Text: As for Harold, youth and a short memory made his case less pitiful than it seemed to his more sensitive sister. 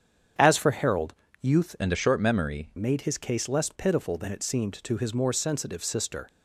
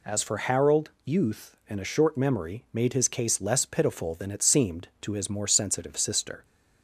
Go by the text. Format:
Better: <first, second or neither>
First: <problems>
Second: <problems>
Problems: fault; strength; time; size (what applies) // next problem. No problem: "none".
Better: second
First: starts louder than the rest; strong; until 1.6 s; 8 dB // changes voice from "and" to "memory"; from 1.7 to 2.6 s; 0.9 s long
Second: none